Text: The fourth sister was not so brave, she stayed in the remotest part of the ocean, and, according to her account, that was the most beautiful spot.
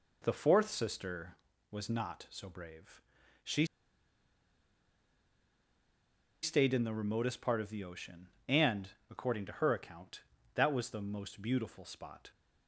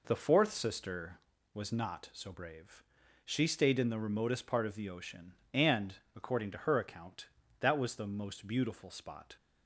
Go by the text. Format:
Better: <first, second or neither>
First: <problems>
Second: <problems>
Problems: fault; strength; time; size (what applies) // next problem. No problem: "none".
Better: second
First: pauses between "she" and "stayed"; strong; at 3.6 s; 2.7 s long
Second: none